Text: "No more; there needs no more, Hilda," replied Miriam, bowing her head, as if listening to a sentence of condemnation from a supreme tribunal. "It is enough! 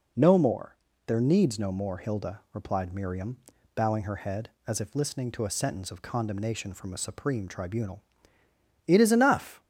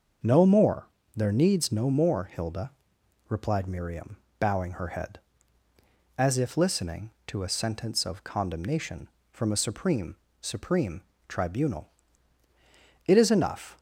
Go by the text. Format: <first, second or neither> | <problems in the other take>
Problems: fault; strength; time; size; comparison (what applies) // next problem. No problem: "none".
first | starts louder than the rest; until 1.4 s; 6.5 dB // says "supreme" twice; at 10.4 s